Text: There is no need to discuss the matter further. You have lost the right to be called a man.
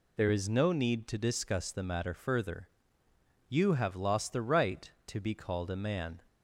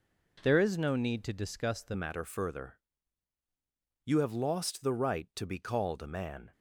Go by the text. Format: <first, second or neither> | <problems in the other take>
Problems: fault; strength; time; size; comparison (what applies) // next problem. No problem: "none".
first | changes voice at "matter"; from 1.9 s on; 4.6 s long